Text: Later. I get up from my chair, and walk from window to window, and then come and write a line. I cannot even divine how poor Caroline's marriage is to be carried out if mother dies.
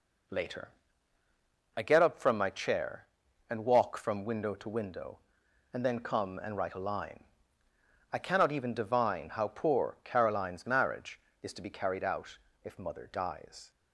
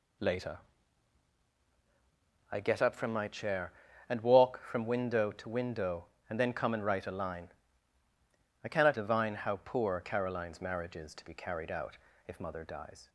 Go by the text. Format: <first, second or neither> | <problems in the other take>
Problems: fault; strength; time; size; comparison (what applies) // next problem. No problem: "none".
first | skips "even"; at 8.9 s // pauses between "out" and "if"; slight; at 11.9 s; 0.30 s long; slight in the first